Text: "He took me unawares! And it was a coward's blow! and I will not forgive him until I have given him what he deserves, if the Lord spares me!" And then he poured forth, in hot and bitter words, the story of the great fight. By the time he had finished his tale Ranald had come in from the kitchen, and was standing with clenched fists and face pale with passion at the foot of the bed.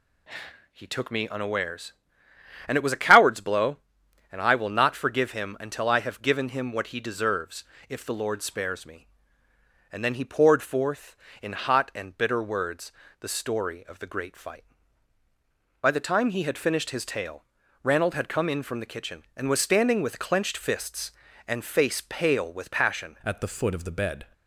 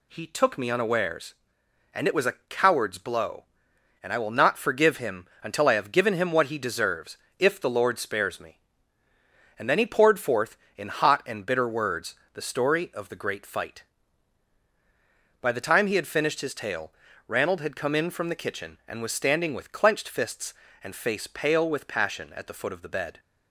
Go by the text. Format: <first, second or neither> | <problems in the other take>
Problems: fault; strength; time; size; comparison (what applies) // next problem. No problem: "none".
second | pauses between "tale" and "Ranald"; at 17.4 s; 0.40 s long; slight in the second // changes voice at "at"; from 23.2 s on; 1.0 s long